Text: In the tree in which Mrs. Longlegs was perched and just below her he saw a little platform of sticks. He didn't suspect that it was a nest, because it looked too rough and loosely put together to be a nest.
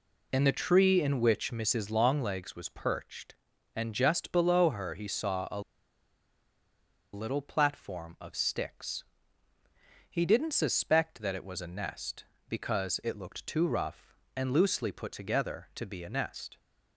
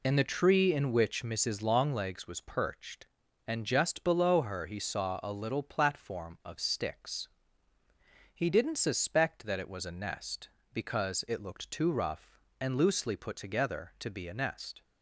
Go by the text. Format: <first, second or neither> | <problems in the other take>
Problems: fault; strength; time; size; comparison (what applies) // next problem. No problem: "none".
second | pauses between "a" and "little"; strong; at 5.5 s; 1.5 s long